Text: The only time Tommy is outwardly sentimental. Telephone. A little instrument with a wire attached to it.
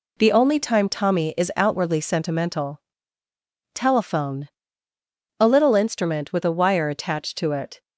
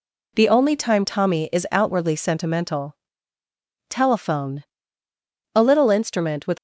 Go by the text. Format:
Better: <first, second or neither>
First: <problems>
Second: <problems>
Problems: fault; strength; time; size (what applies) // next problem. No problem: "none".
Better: first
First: none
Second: stops before "a wire attached to it"; at 6.5 s